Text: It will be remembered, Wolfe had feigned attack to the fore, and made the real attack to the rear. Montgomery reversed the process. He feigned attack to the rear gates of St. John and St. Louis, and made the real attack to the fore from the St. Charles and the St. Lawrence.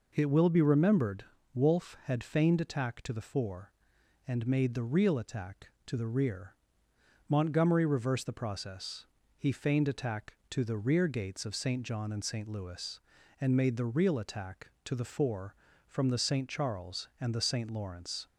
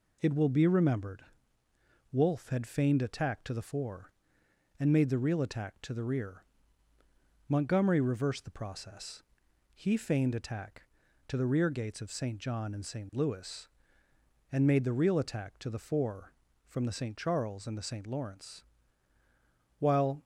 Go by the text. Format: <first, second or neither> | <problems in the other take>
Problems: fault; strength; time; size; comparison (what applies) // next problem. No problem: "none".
first | goes on to say "While"; slight; from 19.7 s on; 0.44 s long